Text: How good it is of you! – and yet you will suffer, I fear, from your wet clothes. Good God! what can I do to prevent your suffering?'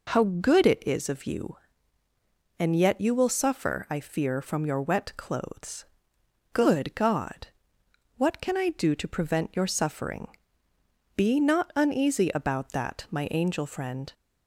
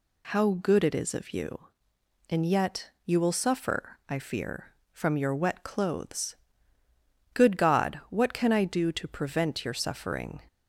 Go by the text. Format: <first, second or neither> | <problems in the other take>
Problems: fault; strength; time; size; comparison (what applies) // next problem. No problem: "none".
second | goes on to say "Be not uneasy about that my angel friend"; strong; from 11.1 s on; 2.9 s long